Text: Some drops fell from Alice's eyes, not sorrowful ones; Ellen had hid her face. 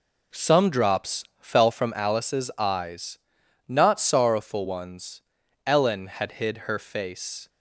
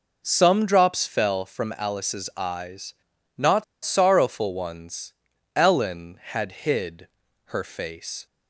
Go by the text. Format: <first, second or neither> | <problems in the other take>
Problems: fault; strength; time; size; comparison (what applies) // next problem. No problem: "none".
first | pauses between "not" and "sorrowful"; slight; at 3.6 s; 0.21 s long // pauses between "hid" and "her"; at 7.0 s; 0.40 s long